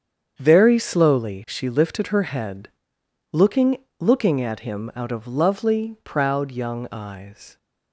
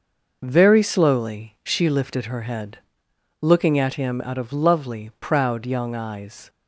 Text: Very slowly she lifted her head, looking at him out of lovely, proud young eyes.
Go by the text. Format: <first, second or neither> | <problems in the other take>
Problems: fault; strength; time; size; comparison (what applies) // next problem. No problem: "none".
second | starts louder than the rest; strong; until 1.3 s; 7.5 dB // says "looking" twice; at 3.9 s